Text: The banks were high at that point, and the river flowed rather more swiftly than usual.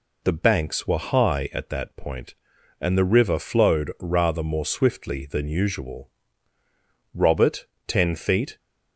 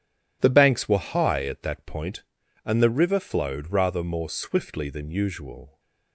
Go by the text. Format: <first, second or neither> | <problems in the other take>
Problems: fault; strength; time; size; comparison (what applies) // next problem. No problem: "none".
second | goes on to say "Robert ten feet"; from 7.1 s on; 1.4 s long